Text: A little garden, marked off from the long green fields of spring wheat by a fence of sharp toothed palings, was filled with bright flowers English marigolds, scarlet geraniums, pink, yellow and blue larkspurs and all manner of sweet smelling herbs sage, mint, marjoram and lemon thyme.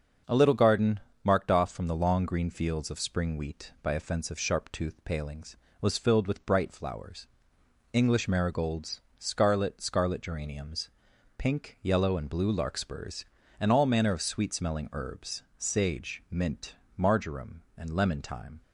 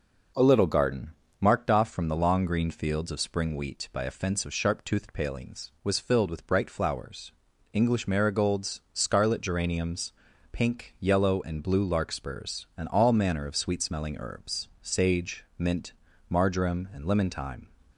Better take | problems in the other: second | starts louder than the rest; until 1.4 s; 6.5 dB // pauses between "flowers" and "English"; noticeable; at 7.2 s; 0.66 s long; also in the second // says "scarlet" twice; at 9.8 s // pauses between "herbs" and "sage"; slight; at 15.4 s; 0.16 s long

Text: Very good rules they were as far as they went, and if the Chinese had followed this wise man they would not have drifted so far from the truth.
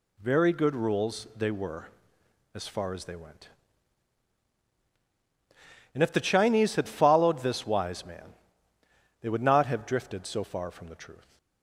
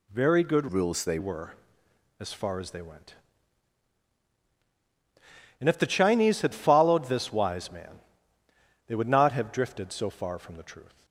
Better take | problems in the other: first | changes voice from "rules" to "they"; from 0.6 to 1.1 s; 0.5 s long // pauses between "man" and "they"; noticeable; at 8.0 s; 0.86 s long; noticeable in the first

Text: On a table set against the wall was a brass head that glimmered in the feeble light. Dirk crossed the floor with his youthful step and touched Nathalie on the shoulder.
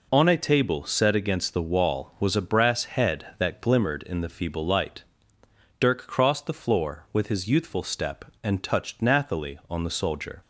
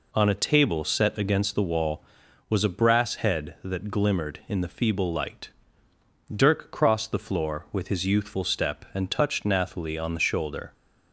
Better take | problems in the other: second | says "soldier" for "shoulder"; at 9.9 s

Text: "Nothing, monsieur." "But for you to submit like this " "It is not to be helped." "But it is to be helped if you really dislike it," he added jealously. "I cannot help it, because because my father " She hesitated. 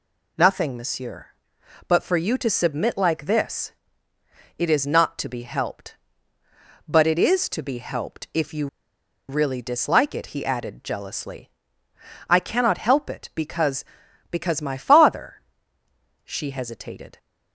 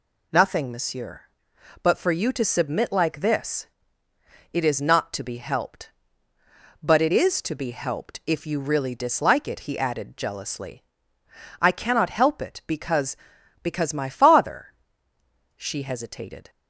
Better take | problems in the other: second | pauses between "you" and "really"; noticeable; at 8.6 s; 0.62 s long

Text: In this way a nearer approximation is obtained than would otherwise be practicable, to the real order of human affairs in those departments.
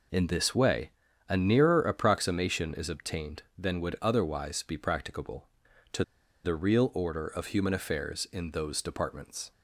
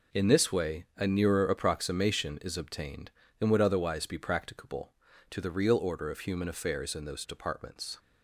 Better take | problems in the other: second | pauses between "way" and "a"; at 0.8 s; 0.38 s long // pauses between "to" and "the"; at 6.0 s; 0.40 s long

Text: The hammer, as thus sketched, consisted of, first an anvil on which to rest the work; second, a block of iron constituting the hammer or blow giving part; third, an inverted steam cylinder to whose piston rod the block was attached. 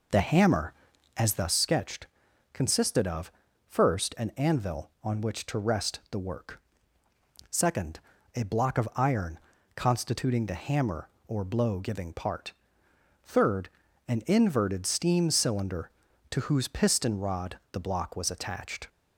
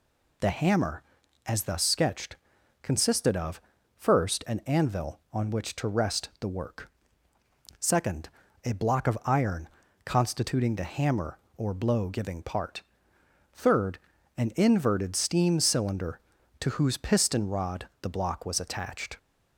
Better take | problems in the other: second | starts louder than the rest; noticeable; until 1.7 s; 4.5 dB // pauses between "iron" and "constituting"; slight; at 9.3 s; 0.36 s long; slight in the second

